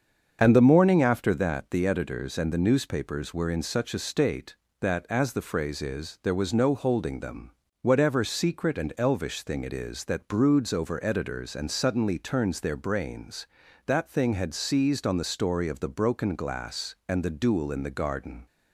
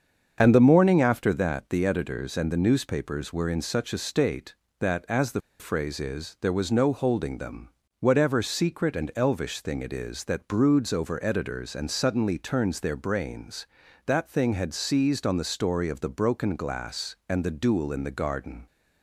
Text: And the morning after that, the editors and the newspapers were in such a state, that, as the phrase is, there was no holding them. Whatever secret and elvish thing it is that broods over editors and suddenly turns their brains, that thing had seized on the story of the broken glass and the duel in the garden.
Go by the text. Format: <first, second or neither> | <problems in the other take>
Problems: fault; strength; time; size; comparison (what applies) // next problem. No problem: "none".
first | starts louder than the rest; until 1.4 s; 7 dB; also in the first // pauses between "the" and "phrase"; slight; at 5.4 s; 0.19 s long